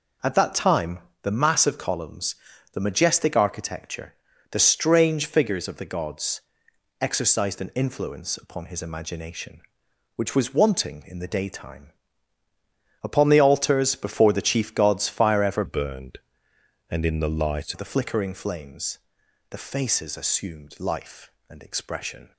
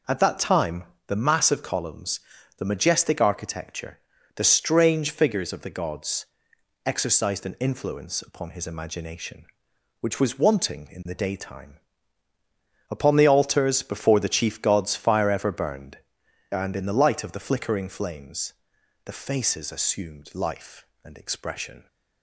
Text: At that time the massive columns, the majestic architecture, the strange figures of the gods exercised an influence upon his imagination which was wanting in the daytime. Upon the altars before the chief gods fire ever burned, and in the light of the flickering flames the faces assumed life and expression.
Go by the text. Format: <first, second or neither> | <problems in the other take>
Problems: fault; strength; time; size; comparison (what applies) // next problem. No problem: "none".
second | pauses between "time" and "the"; slight; at 0.9 s; 0.22 s long; slight in the second // pauses between "gods" and "exercised"; noticeable; at 6.4 s; 0.58 s long; noticeable in the second // changes voice from "burned" to "light"; from 15.6 to 17.7 s; 2.1 s long // pauses between "flames" and "the"; noticeable; at 18.9 s; 0.50 s long; noticeable in the second